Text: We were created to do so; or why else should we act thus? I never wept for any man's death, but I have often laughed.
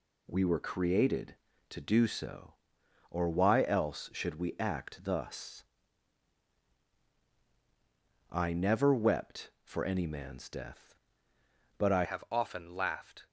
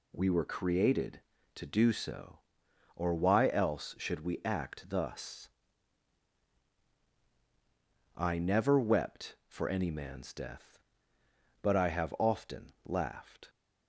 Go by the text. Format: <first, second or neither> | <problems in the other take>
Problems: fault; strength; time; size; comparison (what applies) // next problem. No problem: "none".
second | changes voice at "have"; from 12.0 s on; 1.2 s long